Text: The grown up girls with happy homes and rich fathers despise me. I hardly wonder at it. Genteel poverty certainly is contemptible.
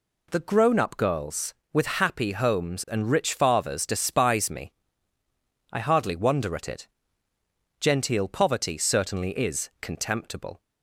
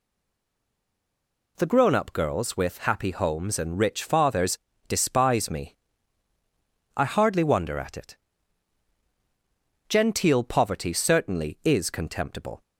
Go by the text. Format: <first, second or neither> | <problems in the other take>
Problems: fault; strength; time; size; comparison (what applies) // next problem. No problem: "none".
first | stays silent before the first word; noticeable; until 1.5 s; 1.5 s long // pauses between "fathers" and "despise"; slight; at 4.5 s; 0.30 s long